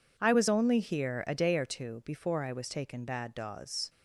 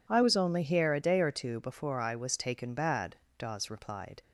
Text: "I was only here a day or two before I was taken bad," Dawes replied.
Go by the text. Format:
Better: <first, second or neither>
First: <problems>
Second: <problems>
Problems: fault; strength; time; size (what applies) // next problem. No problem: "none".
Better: second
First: stops before "replied"; at 3.8 s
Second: none